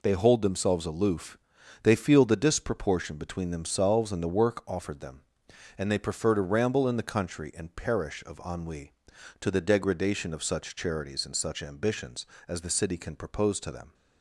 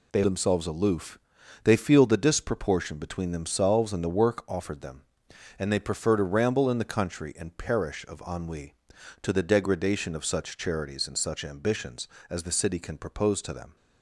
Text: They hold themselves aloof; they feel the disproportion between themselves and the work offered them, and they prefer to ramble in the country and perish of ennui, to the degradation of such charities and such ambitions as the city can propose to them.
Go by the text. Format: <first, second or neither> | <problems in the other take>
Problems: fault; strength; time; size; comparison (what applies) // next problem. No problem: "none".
first | skips "hold"; at 0.2 s